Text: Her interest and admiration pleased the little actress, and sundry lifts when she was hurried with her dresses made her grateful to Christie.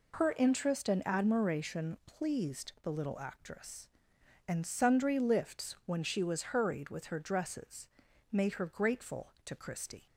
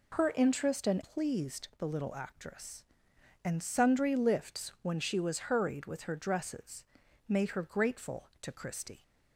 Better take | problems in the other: first | skips "admiration"; at 1.0 s // pauses between "dresses" and "made"; at 6.8 s; 0.44 s long; also in the first

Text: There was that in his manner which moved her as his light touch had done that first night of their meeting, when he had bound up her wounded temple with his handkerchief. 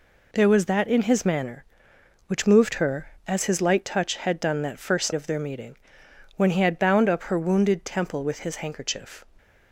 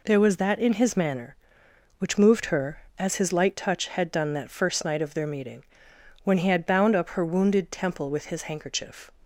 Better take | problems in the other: second | skips "night"; at 5.1 s

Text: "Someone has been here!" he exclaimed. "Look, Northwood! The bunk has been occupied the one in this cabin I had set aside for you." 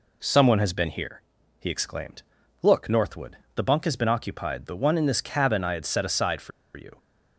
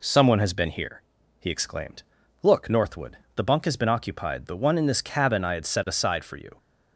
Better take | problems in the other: second | pauses between "for" and "you"; slight; at 6.5 s; 0.24 s long

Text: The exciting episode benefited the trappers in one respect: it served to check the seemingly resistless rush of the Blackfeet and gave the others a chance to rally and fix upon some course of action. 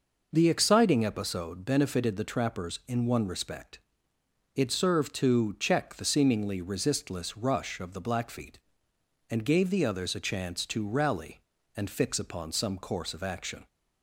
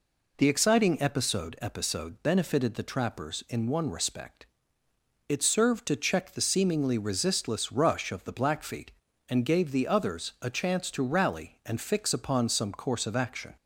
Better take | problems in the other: first | says "episode" twice; at 1.6 s

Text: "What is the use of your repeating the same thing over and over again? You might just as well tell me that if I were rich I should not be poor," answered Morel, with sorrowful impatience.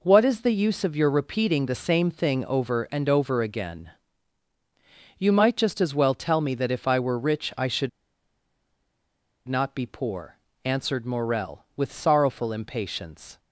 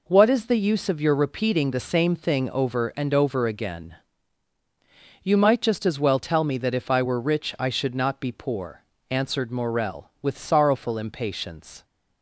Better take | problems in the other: second | pauses between "should" and "not"; strong; at 7.8 s; 1.5 s long

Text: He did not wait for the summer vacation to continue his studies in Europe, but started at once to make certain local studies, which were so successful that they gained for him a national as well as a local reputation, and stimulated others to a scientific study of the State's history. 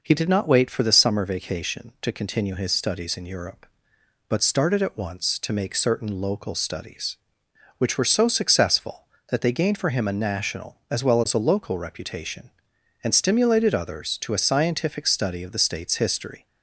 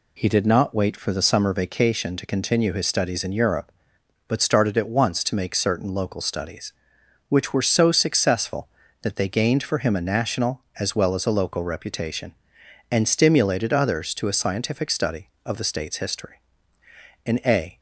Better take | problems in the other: first | goes on to say "In a"; from 17.2 s on; 0.52 s long

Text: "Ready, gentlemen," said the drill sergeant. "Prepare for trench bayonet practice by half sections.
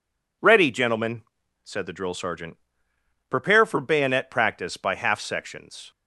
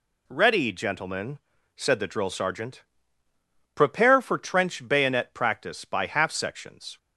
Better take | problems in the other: second | skips "trench"; at 3.8 s

